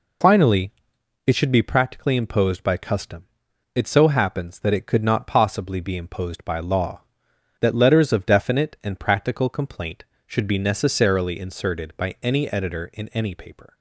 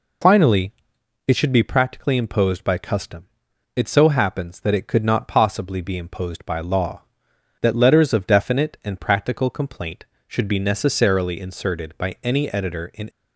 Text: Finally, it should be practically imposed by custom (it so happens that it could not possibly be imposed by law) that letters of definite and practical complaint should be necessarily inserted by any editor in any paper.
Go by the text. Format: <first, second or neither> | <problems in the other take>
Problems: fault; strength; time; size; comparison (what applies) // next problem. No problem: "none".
first | stops before "any paper"; at 13.0 s